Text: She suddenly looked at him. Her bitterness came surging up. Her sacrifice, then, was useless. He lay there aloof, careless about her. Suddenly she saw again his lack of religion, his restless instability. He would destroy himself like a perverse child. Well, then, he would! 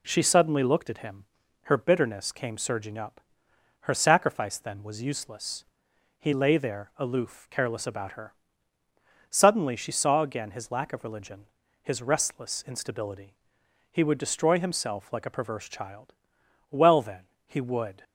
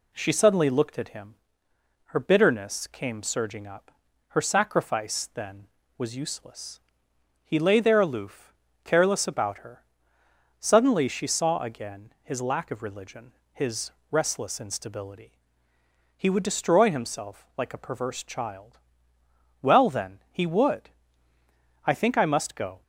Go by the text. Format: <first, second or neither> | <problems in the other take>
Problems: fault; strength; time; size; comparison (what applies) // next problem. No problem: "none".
first | pauses between "his" and "restless"; slight; at 13.8 s; 0.20 s long // goes on to say "I think I must go"; noticeable; from 21.8 s on; 0.96 s long